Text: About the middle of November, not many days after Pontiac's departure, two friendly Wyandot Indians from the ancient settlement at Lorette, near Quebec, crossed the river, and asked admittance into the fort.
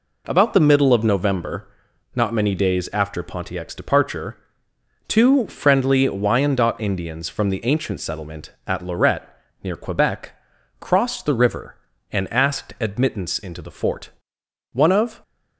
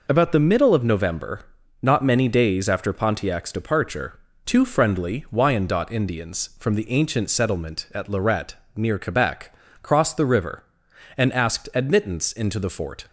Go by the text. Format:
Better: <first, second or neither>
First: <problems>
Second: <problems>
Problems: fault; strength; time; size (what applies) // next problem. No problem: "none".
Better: second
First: goes on to say "One of"; from 14.7 s on; 0.50 s long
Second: none